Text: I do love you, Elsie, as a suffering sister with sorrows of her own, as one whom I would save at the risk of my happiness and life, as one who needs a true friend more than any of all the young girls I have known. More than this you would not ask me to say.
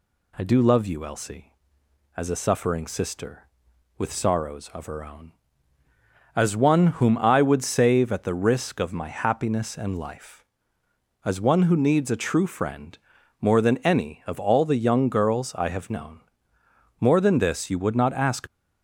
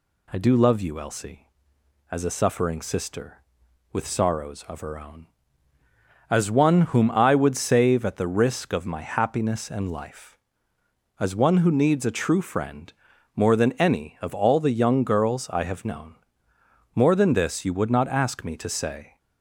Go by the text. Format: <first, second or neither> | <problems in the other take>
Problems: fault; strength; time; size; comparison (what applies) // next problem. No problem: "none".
second | pauses between "friend" and "more"; noticeable; at 12.9 s; 0.46 s long; noticeable in the second // stops before "me to say"; at 18.4 s